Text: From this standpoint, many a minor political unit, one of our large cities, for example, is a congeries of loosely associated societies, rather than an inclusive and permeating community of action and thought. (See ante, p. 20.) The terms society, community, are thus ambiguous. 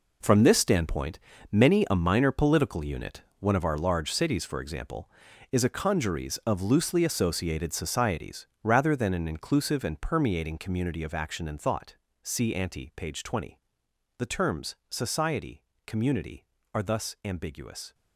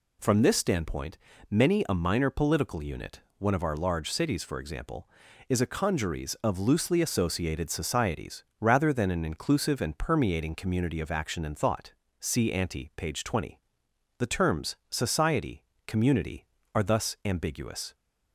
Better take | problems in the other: second | gets quieter; strong; throughout; 11.5 dB // pauses between "terms" and "society"; slight; at 14.7 s; 0.16 s long; slight in the second

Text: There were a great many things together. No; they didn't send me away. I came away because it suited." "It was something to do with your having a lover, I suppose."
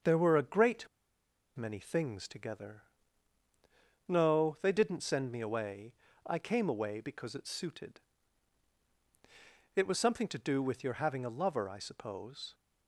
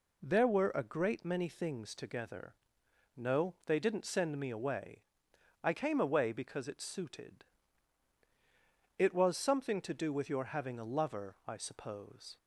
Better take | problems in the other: second | starts louder than the rest; until 1.7 s; 6.5 dB // pauses between "great" and "many"; noticeable; at 0.8 s; 0.68 s long

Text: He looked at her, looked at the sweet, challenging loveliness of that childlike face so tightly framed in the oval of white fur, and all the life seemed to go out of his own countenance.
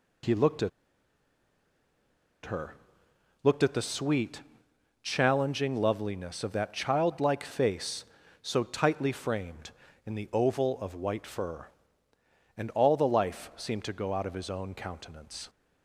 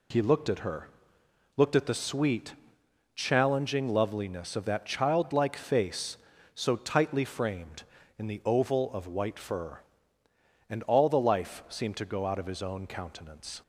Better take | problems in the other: second | pauses between "at" and "her"; strong; at 0.6 s; 1.7 s long

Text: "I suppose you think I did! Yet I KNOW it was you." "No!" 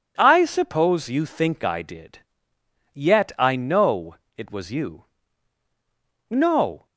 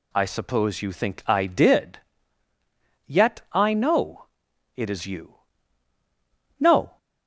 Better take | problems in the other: first | pauses between "KNOW" and "it"; noticeable; at 4.2 s; 0.50 s long; slight in the first // says "is" for "was"; at 4.8 s

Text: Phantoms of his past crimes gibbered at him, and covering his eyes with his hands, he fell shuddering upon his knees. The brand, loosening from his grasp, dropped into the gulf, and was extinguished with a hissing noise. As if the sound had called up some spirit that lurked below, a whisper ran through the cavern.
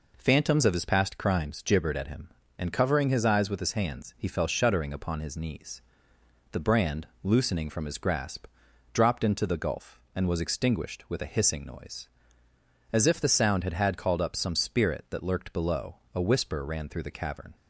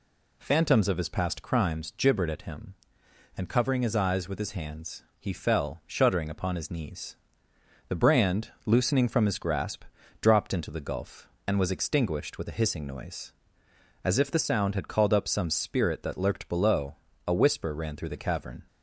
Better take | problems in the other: second | says "had" twice; at 13.7 s

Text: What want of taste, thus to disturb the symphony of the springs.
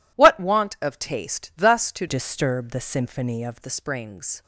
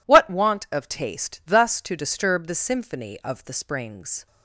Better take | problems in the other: second | changes voice from "disturb" to "of"; from 2.0 to 3.5 s; 1.5 s long

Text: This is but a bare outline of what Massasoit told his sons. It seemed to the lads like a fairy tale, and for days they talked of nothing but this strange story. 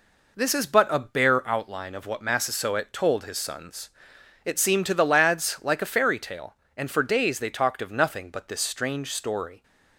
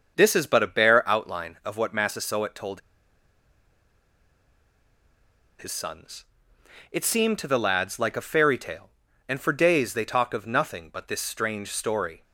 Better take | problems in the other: first | starts louder than the rest; until 1.1 s; 6.5 dB // pauses between "told" and "his"; strong; at 2.8 s; 2.7 s long

